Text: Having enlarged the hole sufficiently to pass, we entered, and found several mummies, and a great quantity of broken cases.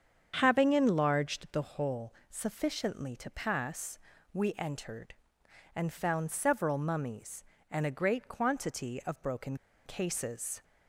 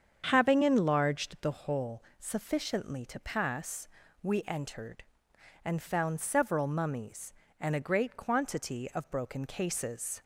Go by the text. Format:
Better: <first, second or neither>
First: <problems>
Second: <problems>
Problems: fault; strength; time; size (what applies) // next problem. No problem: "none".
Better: second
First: starts louder than the rest; strong; until 1.3 s; 7.5 dB // pauses between "hole" and "sufficiently"; slight; at 2.1 s; 0.16 s long // pauses between "broken" and "cases"; slight; at 9.5 s; 0.31 s long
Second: starts louder than the rest; strong; until 1.2 s; 7.5 dB // pauses between "hole" and "sufficiently"; slight; at 2.0 s; 0.16 s long